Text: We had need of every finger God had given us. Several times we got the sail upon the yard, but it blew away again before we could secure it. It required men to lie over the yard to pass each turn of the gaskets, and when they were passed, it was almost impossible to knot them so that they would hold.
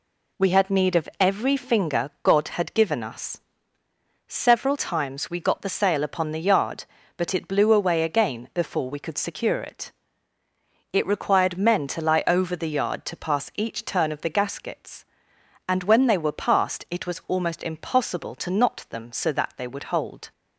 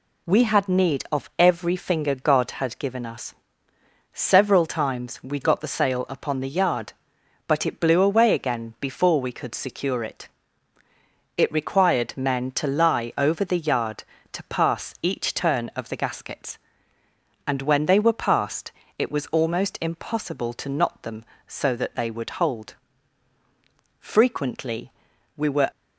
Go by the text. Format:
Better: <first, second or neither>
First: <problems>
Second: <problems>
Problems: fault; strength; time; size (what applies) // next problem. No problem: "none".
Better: first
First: none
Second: goes on to say "Frequently we were"; strong; from 24.0 s on; 1.7 s long